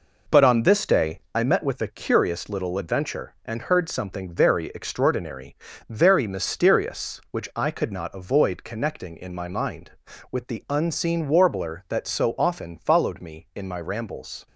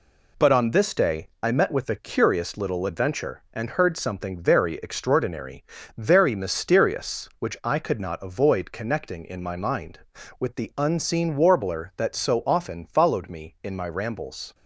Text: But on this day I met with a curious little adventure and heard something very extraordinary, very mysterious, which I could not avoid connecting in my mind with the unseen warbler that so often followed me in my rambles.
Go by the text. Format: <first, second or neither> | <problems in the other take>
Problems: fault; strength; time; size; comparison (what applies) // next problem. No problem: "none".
second | starts louder than the rest; noticeable; until 1.5 s; 4.5 dB // pauses between "day" and "I"; slight; at 1.2 s; 0.16 s long; slight in the second